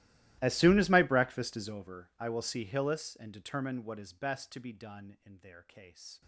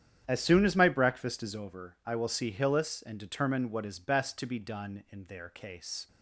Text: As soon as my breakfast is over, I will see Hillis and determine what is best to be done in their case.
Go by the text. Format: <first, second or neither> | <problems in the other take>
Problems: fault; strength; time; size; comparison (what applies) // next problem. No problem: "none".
second | gets quieter; strong; throughout; 25.5 dB // starts louder than the rest; strong; until 1.4 s; 15.5 dB; strong in the second